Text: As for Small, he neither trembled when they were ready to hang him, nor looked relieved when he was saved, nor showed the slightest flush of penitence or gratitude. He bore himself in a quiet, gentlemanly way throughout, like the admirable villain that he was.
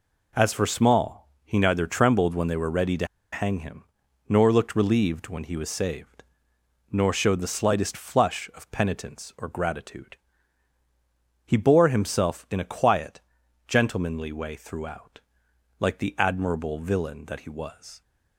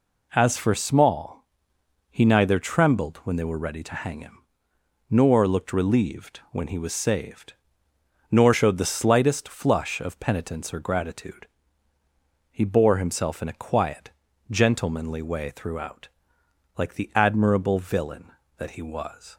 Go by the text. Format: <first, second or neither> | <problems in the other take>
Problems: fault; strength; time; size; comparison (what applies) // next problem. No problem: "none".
second | pauses between "to" and "hang"; slight; at 3.0 s; 0.26 s long